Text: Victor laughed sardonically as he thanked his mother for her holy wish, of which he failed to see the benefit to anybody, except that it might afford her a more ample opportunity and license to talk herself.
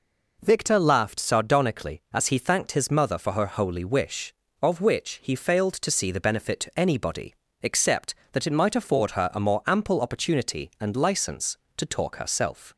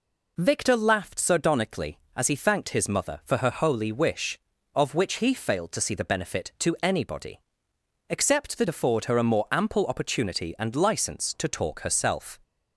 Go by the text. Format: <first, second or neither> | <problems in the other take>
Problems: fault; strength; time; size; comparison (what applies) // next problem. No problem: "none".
first | skips "it might"; at 8.6 s